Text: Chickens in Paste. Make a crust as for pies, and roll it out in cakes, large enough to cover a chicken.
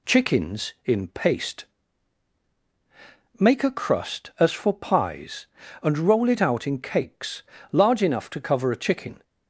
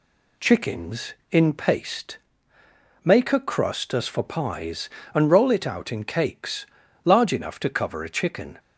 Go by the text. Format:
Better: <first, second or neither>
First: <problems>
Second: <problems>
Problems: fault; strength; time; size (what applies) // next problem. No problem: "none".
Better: neither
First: none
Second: none